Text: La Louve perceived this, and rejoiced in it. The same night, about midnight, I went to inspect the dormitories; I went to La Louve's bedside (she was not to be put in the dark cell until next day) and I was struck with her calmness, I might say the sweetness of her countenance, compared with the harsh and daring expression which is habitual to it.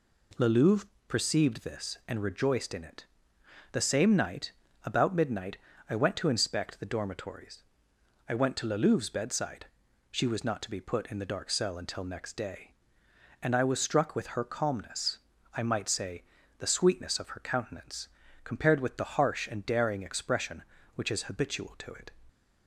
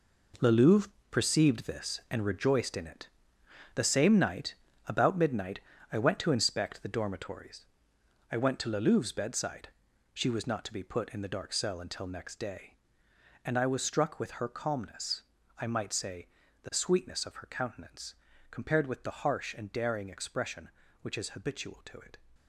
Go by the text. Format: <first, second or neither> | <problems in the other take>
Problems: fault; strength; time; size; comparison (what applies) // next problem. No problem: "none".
first | gets quieter; strong; throughout; 10.5 dB // pauses between "Louve" and "perceived"; slight; at 0.8 s; 0.22 s long; slight in the first // pauses between "say" and "the"; slight; at 16.2 s; 0.36 s long; slight in the first